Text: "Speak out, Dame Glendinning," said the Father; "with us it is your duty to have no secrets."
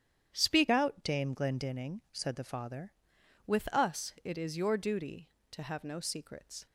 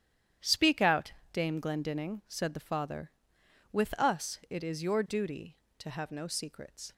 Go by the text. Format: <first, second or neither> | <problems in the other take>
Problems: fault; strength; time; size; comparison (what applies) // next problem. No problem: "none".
second | starts louder than the rest; strong; until 1.3 s; 9.5 dB; strong in the second // changes voice from "out" to "Father"; from 0.7 to 2.9 s; 2.2 s long